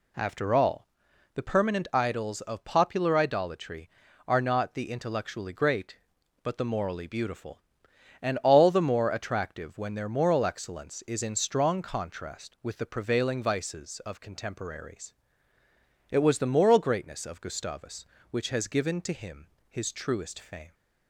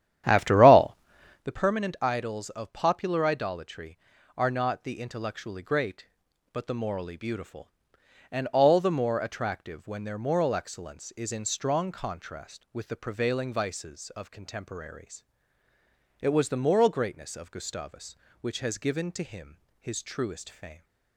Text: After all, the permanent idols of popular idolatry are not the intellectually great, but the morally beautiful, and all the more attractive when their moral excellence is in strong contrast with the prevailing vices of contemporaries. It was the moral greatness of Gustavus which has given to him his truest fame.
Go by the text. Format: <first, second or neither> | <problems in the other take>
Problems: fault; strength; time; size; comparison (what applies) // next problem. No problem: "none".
first | starts louder than the rest; strong; until 1.5 s; 11 dB // pauses between "him" and "his"; slight; at 19.5 s; 0.24 s long; slight in the first